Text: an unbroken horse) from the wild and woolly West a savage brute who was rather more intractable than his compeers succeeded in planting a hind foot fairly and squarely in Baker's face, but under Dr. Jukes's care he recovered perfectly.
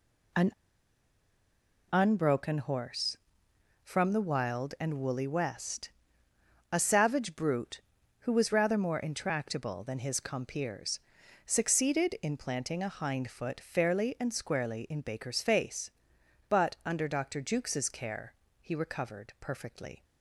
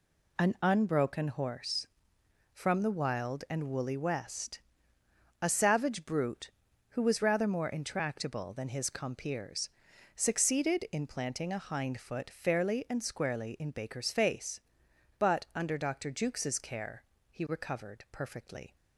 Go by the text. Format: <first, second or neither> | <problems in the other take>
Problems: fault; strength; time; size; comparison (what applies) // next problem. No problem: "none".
second | pauses between "an" and "unbroken"; strong; at 0.5 s; 1.4 s long // pauses between "West" and "a"; noticeable; at 5.8 s; 0.82 s long; noticeable in the second // pauses between "compeers" and "succeeded"; at 10.9 s; 0.44 s long; also in the second // pauses between "care" and "he"; slight; at 18.3 s; 0.26 s long; slight in the second